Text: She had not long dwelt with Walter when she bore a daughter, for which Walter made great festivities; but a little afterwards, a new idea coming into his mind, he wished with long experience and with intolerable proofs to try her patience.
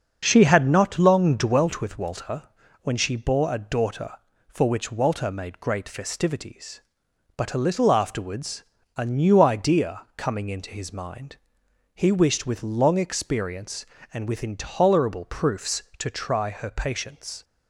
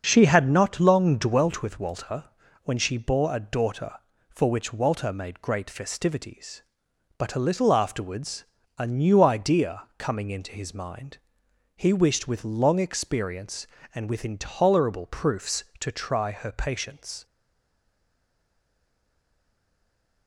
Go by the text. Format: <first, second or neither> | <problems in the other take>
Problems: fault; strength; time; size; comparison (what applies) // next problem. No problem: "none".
first | starts louder than the rest; until 1.0 s; 6.5 dB; also in the first // pauses between "Walter" and "when"; slight; at 2.2 s; 0.36 s long; slight in the first // stays silent after the last word; strong; from 17.2 s on; 3.0 s long